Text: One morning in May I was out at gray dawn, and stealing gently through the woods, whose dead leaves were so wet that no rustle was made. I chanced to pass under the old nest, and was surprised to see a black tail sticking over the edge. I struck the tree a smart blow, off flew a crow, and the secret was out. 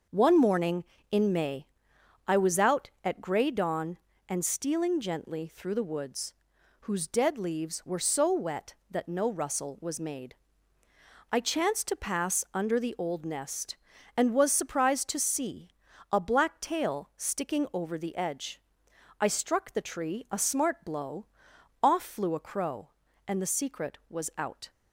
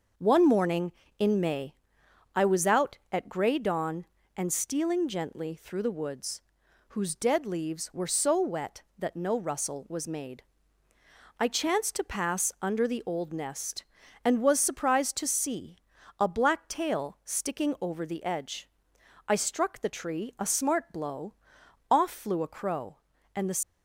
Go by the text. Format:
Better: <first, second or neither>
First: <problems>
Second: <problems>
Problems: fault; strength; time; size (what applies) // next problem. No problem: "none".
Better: first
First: pauses between "May" and "I"; noticeable; at 1.6 s; 0.60 s long // pauses between "see" and "a"; at 15.7 s; 0.38 s long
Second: pauses between "May" and "I"; noticeable; at 1.7 s; 0.60 s long // pauses between "see" and "a"; at 15.7 s; 0.38 s long // stops before "secret was out"; at 23.6 s